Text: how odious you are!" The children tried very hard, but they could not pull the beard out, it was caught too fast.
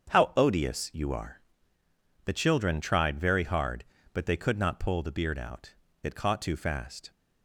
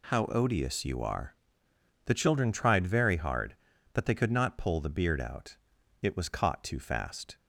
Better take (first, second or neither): second